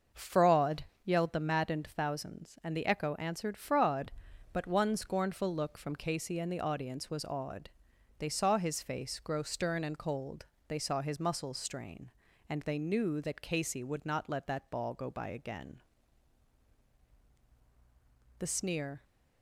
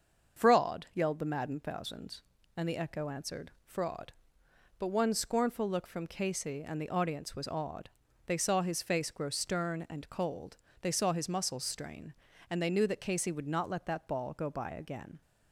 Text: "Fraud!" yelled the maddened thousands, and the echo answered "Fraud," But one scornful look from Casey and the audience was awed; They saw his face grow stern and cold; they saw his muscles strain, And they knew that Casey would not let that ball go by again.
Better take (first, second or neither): second